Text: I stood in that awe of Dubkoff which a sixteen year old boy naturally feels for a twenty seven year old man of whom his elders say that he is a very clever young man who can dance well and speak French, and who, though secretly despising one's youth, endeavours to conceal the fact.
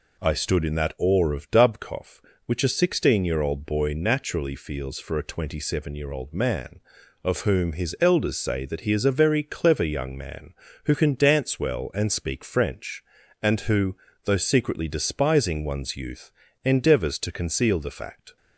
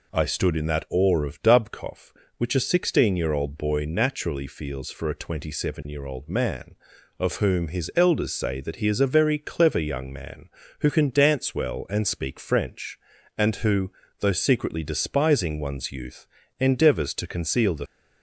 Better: first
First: none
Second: stops before "fact"; at 17.8 s

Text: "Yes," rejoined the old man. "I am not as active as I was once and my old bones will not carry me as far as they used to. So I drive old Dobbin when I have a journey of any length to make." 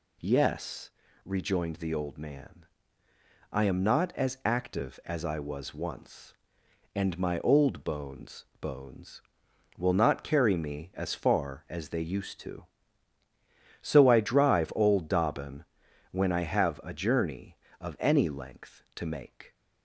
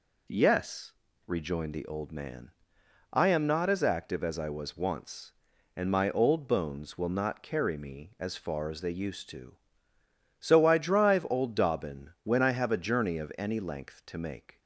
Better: second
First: says "bones" twice; at 8.5 s // pauses between "Dobbin" and "when"; noticeable; at 15.6 s; 0.48 s long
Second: none

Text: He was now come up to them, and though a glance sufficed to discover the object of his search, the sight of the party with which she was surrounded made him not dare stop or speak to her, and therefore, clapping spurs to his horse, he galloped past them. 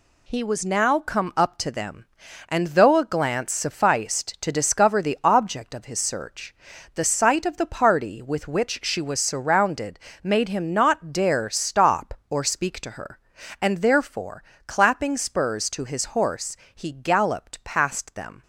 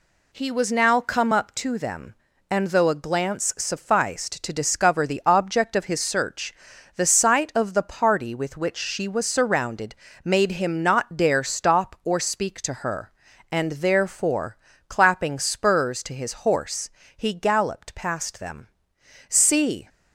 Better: first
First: pauses between "surrounded" and "made"; slight; at 9.9 s; 0.24 s long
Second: pauses between "surrounded" and "made"; slight; at 9.9 s; 0.30 s long // goes on to say "See"; from 19.2 s on; 0.60 s long

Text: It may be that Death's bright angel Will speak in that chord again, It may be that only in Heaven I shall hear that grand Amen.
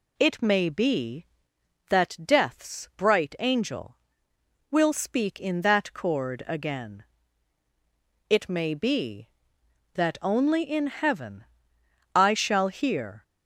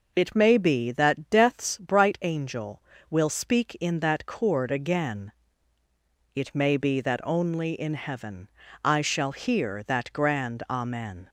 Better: second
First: pauses between "Heaven" and "I"; noticeable; at 11.4 s; 0.71 s long // stops before "that grand Amen"; at 13.2 s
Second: pauses between "Heaven" and "I"; slight; at 8.4 s; 0.34 s long

